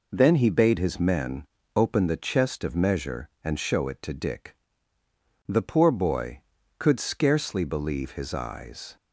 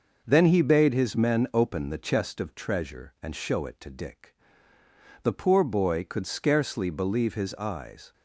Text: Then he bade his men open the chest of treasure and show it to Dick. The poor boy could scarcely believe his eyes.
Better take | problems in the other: second | pauses between "men" and "open"; slight; at 1.4 s; 0.30 s long // says "measure" for "treasure"; at 2.7 s

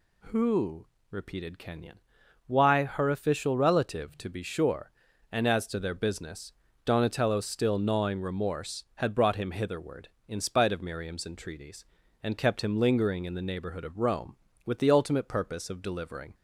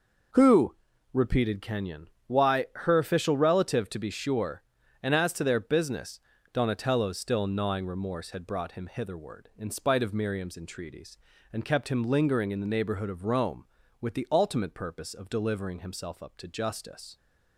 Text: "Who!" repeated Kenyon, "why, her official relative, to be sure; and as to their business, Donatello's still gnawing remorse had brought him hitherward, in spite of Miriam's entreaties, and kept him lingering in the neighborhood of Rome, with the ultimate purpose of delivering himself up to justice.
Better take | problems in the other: second | stops before "himself up to justice"; at 16.3 s

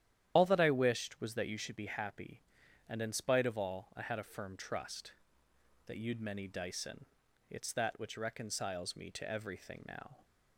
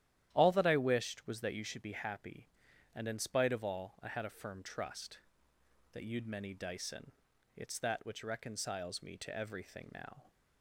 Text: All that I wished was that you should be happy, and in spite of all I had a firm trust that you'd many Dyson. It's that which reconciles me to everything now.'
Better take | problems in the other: second | loses the start of "All"; at 0.3 s; 95 ms // starts louder than the rest; strong; until 1.3 s; 10.5 dB; strong in the second

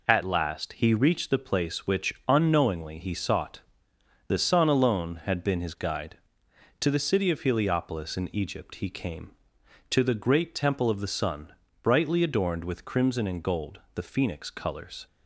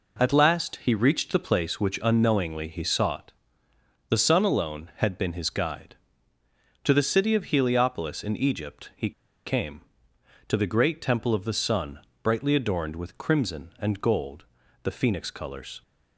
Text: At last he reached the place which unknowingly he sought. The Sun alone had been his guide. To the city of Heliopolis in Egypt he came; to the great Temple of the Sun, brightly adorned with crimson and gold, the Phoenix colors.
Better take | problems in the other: first | pauses between "he" and "came"; at 9.0 s; 0.37 s long

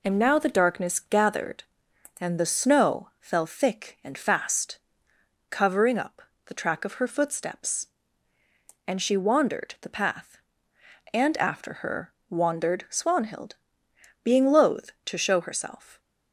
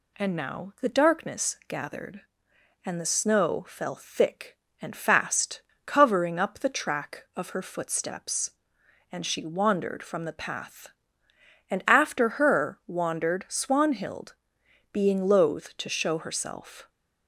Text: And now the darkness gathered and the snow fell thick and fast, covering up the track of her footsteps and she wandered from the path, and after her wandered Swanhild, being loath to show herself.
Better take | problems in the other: second | pauses between "up" and "the"; slight; at 6.2 s; 0.24 s long // skips "from"; at 9.7 s // pauses between "her" and "wandered"; slight; at 12.1 s; 0.16 s long

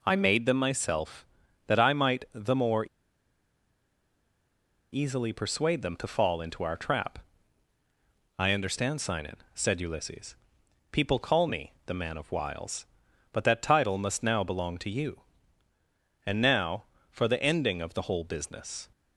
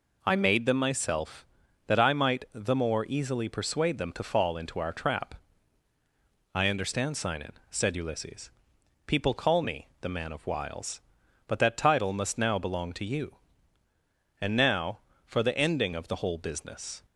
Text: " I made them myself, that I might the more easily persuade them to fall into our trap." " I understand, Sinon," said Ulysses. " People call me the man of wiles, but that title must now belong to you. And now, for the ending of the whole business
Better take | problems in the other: second | pauses between "more" and "easily"; strong; at 2.8 s; 2.0 s long // pauses between "me" and "the"; slight; at 11.7 s; 0.16 s long; slight in the second

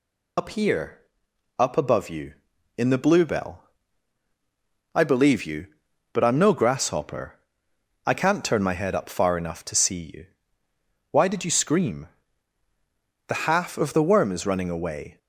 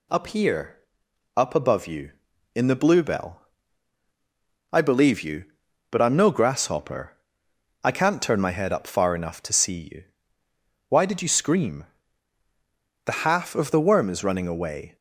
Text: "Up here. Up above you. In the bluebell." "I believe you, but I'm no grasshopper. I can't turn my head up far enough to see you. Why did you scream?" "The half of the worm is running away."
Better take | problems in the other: second | loses the start of "Up"; at 0.3 s; 45 ms

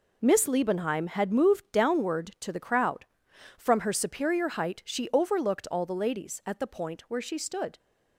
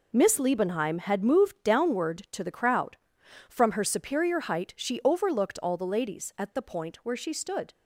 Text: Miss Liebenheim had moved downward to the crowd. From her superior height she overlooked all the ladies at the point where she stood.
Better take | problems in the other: neither | none

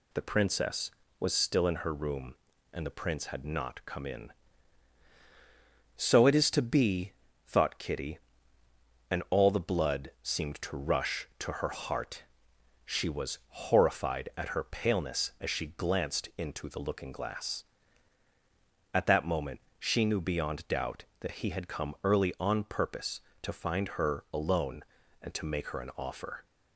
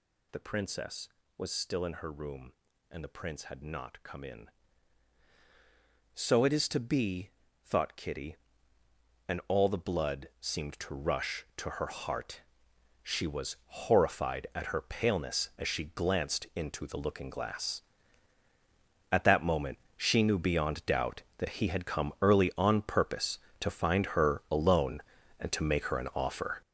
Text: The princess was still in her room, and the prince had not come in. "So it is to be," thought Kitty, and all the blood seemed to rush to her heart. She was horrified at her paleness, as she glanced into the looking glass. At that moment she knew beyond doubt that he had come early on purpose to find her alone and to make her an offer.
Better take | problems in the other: first | gets louder; strong; throughout; 10 dB // pauses between "moment" and "she"; slight; at 19.7 s; 0.18 s long; slight in the first

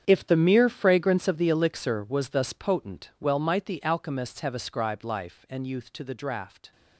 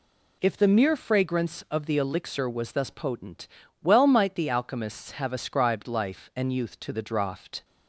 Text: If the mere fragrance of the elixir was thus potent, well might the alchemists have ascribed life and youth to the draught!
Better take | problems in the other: second | gets quieter; strong; throughout; 15 dB

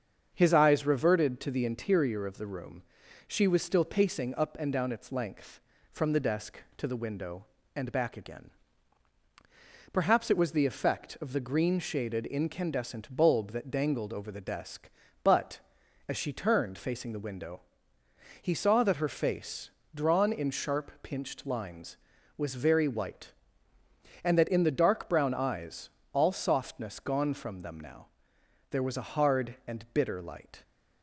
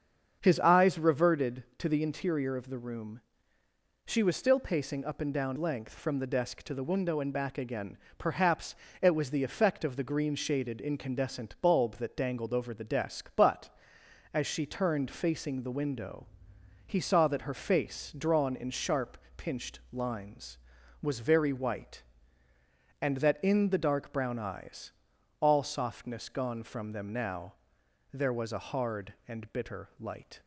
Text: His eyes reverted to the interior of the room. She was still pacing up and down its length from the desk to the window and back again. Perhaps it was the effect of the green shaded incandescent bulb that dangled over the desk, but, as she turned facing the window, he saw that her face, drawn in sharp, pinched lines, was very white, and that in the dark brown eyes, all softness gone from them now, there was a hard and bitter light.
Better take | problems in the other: first | starts louder than the rest; until 1.4 s; 7 dB; also in the first // skips "its"; at 5.5 s // pauses between "Perhaps" and "it"; slight; at 8.7 s; 0.26 s long

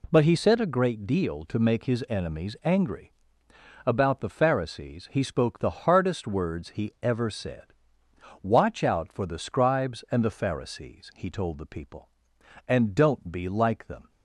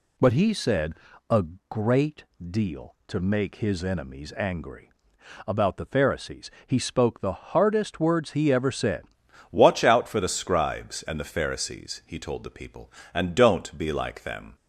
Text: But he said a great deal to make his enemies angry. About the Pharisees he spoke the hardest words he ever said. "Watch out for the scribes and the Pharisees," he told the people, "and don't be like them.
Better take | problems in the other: first | pauses between "said" and "a"; slight; at 0.9 s; 0.36 s long // pauses between "a" and "great"; slight; at 1.4 s; 0.24 s long // pauses between "great" and "deal"; slight; at 2.2 s; 0.26 s long // pauses between "Pharisees" and "he"; slight; at 6.4 s; 0.16 s long // changes voice at "Watch"; from 9.5 s on; 5.0 s long

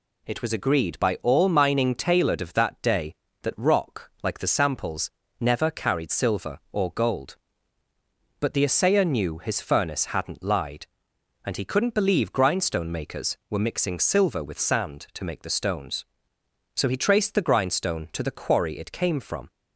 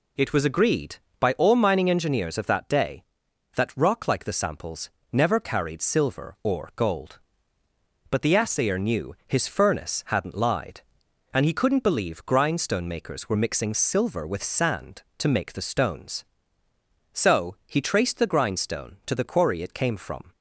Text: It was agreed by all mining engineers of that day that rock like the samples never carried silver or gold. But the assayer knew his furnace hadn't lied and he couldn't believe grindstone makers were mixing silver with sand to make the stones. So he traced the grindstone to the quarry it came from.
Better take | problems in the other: second | says "tailored" for "engineers"; at 1.9 s // pauses between "samples" and "never"; slight; at 5.0 s; 0.30 s long; slight in the second

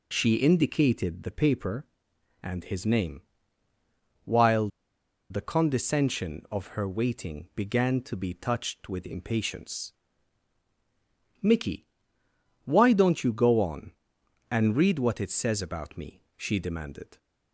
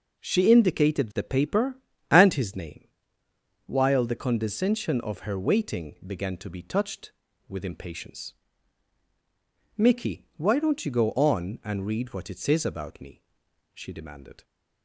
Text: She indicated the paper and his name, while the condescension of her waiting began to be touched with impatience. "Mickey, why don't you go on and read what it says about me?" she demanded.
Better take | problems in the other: second | pauses between "while" and "the"; noticeable; at 4.6 s; 0.62 s long

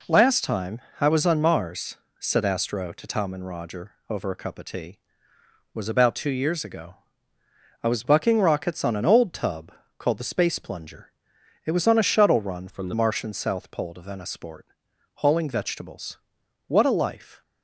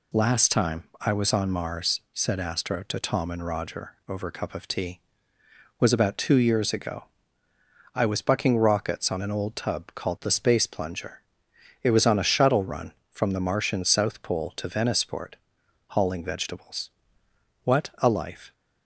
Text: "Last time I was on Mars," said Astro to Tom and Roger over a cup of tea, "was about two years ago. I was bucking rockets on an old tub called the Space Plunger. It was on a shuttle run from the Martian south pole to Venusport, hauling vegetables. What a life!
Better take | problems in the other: second | pauses between "time" and "I"; slight; at 0.7 s; 0.20 s long; slight in the second // pauses between "Roger" and "over"; slight; at 3.9 s; 0.18 s long // pauses between "tub" and "called"; slight; at 9.6 s; 0.30 s long // changes voice from "from" to "the"; from 12.6 to 12.9 s; 0.3 s long

